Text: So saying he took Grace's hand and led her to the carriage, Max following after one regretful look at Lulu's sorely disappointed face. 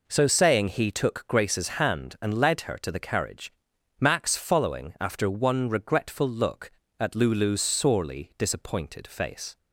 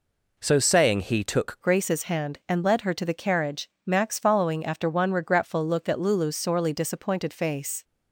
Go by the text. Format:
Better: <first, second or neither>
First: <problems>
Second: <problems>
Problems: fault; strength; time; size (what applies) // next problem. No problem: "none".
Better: first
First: none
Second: changes voice at "Grace's"; from 1.6 s on; 6.2 s long